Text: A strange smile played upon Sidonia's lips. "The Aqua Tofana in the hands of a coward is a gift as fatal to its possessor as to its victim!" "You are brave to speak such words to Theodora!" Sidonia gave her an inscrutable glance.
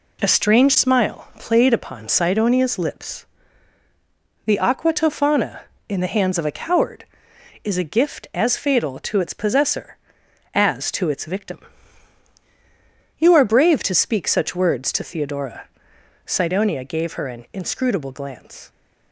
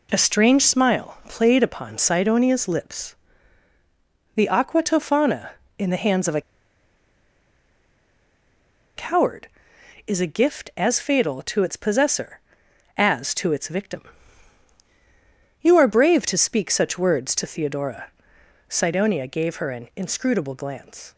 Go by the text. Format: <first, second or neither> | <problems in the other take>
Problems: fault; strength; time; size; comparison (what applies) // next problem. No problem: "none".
first | pauses between "a" and "coward"; strong; at 6.3 s; 2.5 s long